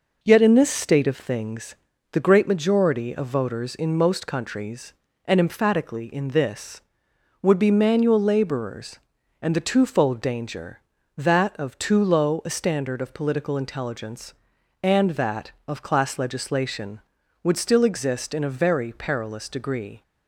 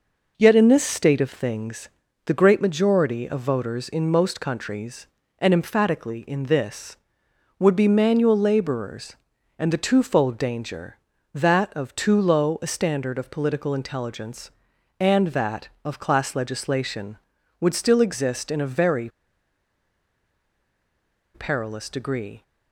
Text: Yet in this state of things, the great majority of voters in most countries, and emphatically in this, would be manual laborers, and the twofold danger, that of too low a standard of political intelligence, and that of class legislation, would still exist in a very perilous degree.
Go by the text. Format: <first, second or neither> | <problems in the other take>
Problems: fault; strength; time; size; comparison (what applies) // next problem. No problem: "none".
first | pauses between "very" and "perilous"; strong; at 19.0 s; 2.2 s long